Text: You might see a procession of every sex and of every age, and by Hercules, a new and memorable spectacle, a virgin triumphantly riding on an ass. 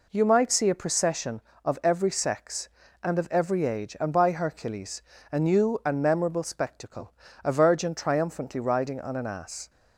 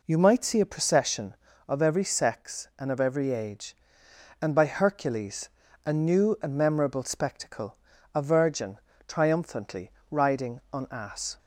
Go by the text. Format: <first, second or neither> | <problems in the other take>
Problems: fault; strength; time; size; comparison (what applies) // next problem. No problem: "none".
first | pauses between "virgin" and "triumphantly"; slight; at 8.7 s; 0.28 s long // pauses between "triumphantly" and "riding"; slight; at 9.9 s; 0.18 s long // skips "an"; at 10.8 s